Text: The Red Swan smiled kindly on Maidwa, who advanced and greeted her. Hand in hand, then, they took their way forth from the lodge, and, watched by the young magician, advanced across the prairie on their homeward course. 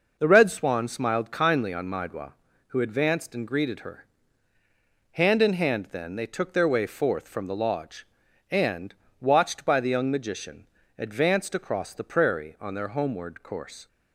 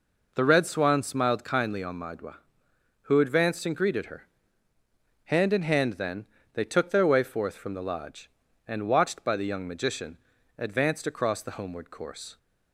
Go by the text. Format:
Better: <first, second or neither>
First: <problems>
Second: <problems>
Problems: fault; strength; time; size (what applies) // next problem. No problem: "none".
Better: first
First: none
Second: skips "prairie on their"; at 11.5 s